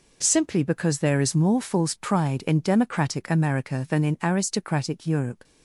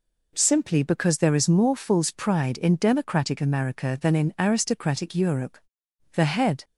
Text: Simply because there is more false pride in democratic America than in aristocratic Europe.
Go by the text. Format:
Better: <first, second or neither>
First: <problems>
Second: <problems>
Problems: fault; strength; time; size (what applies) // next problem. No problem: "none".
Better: first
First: none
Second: goes on to say "The head"; from 6.1 s on; 0.50 s long